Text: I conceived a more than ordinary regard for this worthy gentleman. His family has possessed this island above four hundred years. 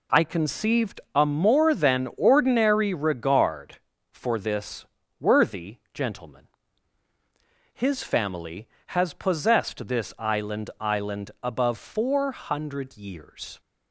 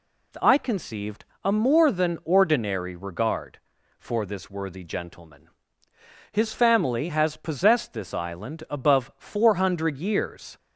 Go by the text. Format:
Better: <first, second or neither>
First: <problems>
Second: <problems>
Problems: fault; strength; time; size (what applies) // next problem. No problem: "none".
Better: second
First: pauses between "conceived" and "a"; slight; at 0.9 s; 0.16 s long // pauses between "this" and "worthy"; slight; at 4.8 s; 0.36 s long // pauses between "worthy" and "gentleman"; slight; at 5.7 s; 0.16 s long // says "island" twice; at 10.7 s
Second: pauses between "conceived" and "a"; slight; at 1.2 s; 0.18 s long